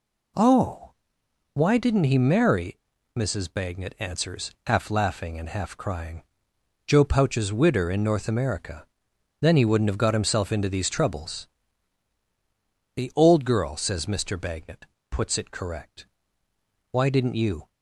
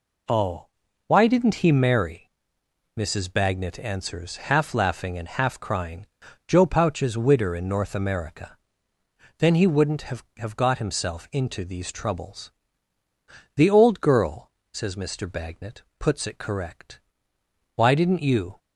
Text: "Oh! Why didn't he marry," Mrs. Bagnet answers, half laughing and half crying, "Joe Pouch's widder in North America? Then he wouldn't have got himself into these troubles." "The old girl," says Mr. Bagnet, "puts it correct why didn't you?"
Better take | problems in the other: first | says "have" twice; at 10.3 s // pauses between "correct" and "why"; noticeable; at 17.0 s; 0.74 s long; noticeable in the first

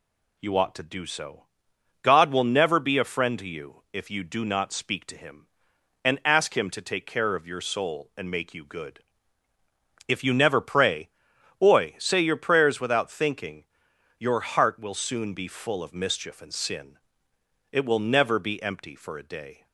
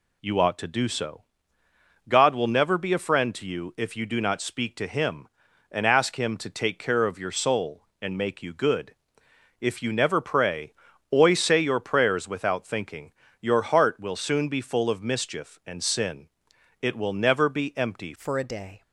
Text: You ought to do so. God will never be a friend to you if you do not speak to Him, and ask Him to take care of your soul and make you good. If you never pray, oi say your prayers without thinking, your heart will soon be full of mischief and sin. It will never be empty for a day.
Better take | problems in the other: first | changes voice at "for"; from 18.1 s on; 0.7 s long

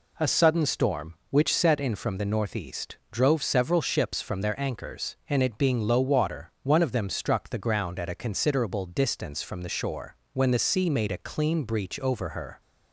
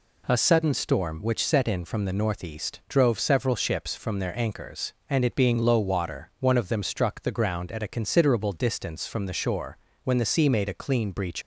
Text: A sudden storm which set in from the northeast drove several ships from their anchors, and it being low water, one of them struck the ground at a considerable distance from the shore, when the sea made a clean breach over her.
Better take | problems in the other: first | stops before "over her"; at 11.4 s

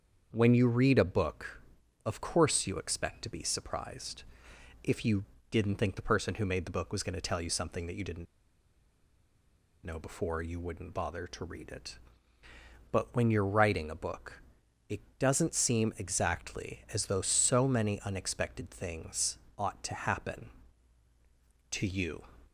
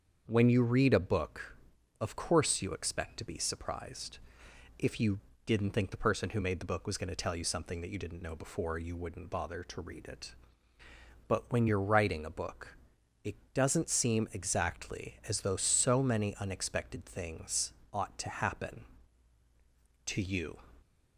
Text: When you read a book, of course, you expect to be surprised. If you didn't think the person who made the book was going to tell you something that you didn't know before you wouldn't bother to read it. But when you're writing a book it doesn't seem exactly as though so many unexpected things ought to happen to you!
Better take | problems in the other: second | starts louder than the rest; until 1.3 s; 7 dB; also in the second // pauses between "you" and "didn't"; slight; at 5.2 s; 0.26 s long; slight in the second // pauses between "didn't" and "know"; strong; at 8.2 s; 1.6 s long // pauses between "book" and "it"; noticeable; at 14.4 s; 0.50 s long; noticeable in the second // pauses between "it" and "doesn't"; slight; at 15.0 s; 0.18 s long; slight in the second // pauses between "things" and "ought"; slight; at 19.3 s; 0.22 s long; slight in the second

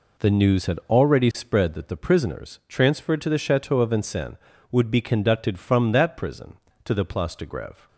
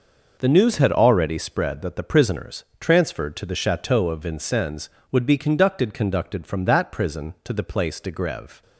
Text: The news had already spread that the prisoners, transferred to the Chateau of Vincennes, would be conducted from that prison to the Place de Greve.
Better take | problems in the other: first | says "conducted" twice; at 5.9 s

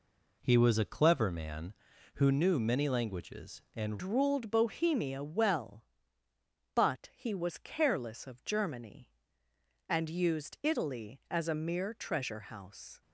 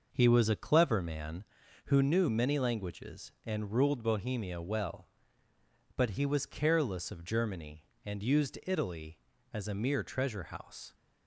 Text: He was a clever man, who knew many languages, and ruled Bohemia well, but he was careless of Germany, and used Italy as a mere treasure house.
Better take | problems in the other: second | changes voice at "ruled"; from 4.0 s on; 9.0 s long

